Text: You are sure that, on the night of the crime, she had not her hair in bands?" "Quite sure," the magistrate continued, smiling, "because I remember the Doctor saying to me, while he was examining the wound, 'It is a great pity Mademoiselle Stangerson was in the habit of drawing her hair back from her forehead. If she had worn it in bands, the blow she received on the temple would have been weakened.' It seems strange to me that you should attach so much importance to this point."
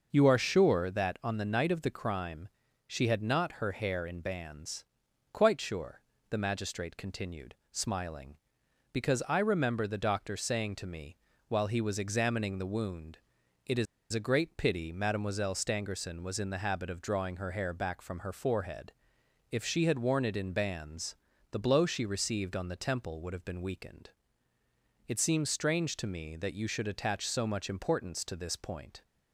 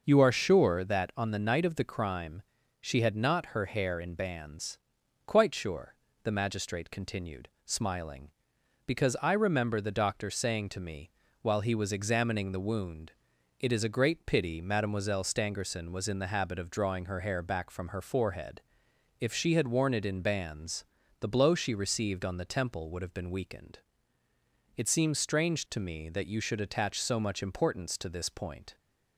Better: second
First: pauses between "is" and "a"; slight; at 13.8 s; 0.27 s long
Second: none

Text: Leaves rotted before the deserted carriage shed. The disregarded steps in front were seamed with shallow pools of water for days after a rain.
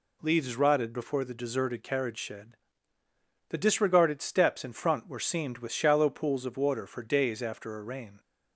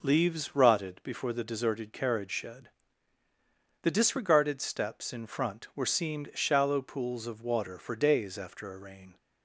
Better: first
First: none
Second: skips "with"; at 6.3 s

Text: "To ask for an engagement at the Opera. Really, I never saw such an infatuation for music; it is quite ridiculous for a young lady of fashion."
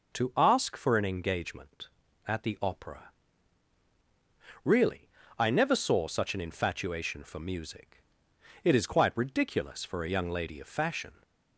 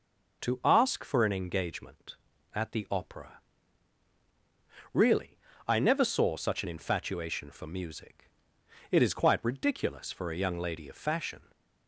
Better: neither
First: none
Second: none

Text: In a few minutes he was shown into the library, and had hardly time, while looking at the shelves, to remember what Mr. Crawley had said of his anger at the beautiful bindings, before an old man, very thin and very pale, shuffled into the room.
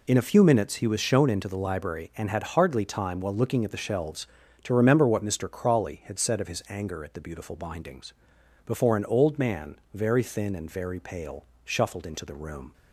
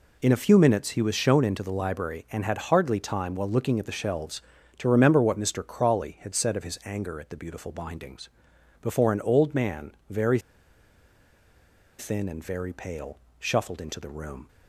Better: first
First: none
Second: pauses between "very" and "thin"; strong; at 10.4 s; 1.5 s long

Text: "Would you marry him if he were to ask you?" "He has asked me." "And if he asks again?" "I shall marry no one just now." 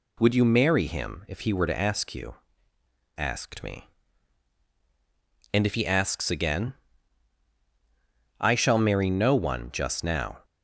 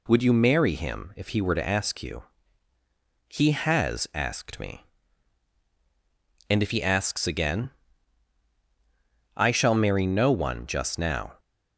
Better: second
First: skips "He has"; at 2.7 s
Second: none

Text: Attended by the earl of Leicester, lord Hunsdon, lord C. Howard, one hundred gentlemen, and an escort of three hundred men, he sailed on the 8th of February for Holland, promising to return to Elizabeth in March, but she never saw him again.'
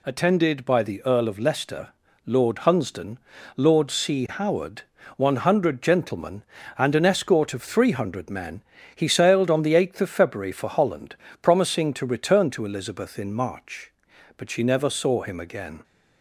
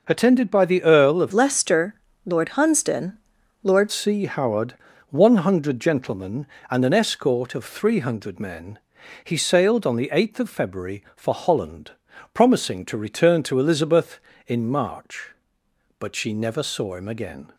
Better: first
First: none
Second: changes voice from "Leicester" to "lord"; from 1.3 to 3.9 s; 2.6 s long

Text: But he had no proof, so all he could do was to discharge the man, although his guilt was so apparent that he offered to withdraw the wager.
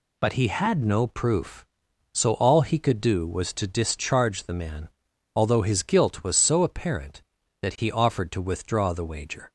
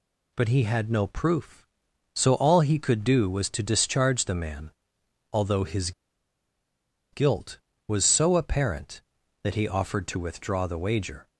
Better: first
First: none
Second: pauses between "his" and "guilt"; at 5.9 s; 1.2 s long

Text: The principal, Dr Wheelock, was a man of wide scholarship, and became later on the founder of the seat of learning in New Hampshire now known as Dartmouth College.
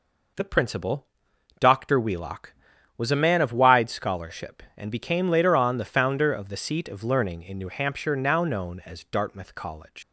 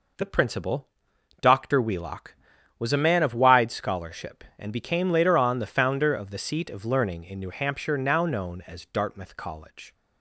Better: second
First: leaves "College" unfinished; at 10.0 s; 90 ms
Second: none

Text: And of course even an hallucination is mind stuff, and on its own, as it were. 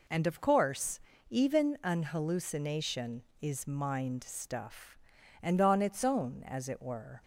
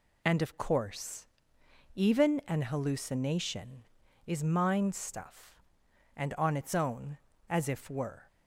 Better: first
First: pauses between "course" and "even"; slight; at 0.9 s; 0.32 s long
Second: pauses between "course" and "even"; noticeable; at 1.2 s; 0.68 s long // says "if" for "it"; at 7.6 s

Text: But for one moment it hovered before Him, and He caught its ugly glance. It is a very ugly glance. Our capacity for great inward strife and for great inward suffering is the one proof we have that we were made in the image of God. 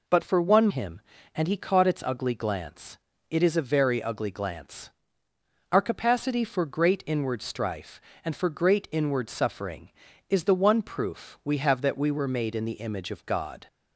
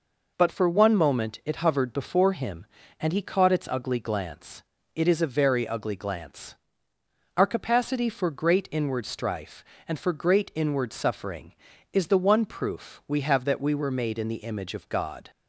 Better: second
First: skips "moment it hovered before"; at 0.6 s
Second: none

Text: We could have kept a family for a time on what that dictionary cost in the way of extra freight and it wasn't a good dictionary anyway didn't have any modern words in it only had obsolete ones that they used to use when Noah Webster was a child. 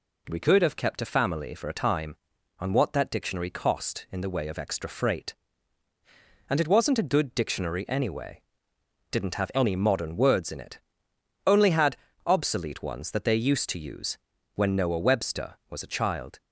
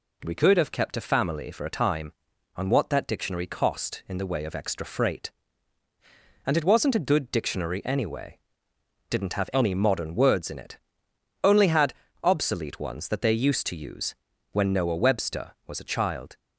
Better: neither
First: pauses between "anyway" and "didn't"; noticeable; at 8.4 s; 0.68 s long // pauses between "it" and "only"; noticeable; at 10.7 s; 0.68 s long // pauses between "had" and "obsolete"; slight; at 11.9 s; 0.30 s long // pauses between "use" and "when"; at 14.1 s; 0.38 s long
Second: pauses between "anyway" and "didn't"; noticeable; at 8.3 s; 0.70 s long // pauses between "it" and "only"; noticeable; at 10.7 s; 0.66 s long // pauses between "had" and "obsolete"; slight; at 11.9 s; 0.30 s long // pauses between "use" and "when"; at 14.1 s; 0.38 s long

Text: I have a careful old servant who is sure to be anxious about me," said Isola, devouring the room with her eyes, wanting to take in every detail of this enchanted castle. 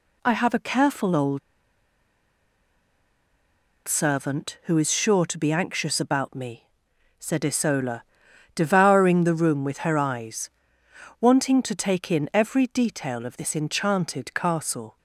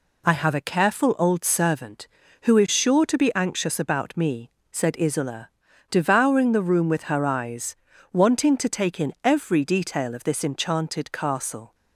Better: second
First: pauses between "old" and "servant"; strong; at 1.3 s; 2.4 s long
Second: none

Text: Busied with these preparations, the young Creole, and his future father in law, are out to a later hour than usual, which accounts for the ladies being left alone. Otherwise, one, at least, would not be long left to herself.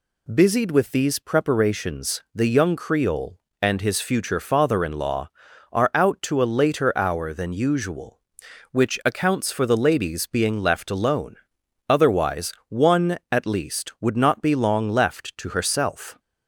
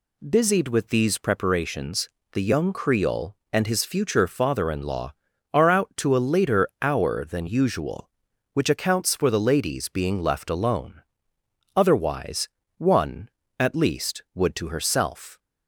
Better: first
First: none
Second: skips "not be long left"; at 14.5 s

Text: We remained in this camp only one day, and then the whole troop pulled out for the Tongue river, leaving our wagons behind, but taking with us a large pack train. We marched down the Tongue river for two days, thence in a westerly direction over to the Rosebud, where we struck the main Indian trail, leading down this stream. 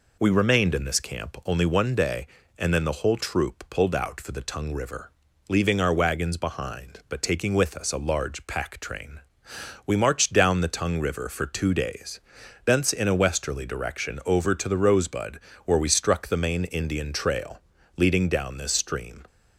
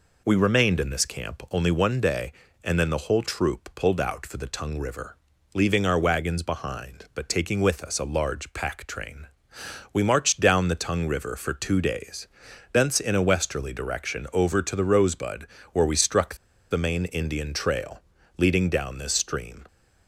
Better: first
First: none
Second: pauses between "struck" and "the"; slight; at 16.3 s; 0.35 s long

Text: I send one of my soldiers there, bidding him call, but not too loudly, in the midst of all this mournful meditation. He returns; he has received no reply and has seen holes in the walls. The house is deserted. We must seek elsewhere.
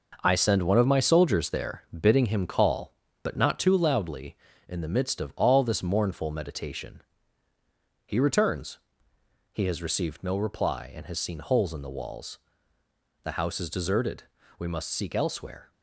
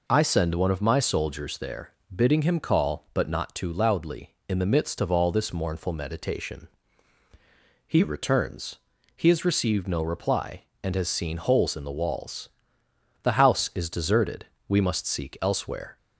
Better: second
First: gets quieter; throughout; 7 dB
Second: none

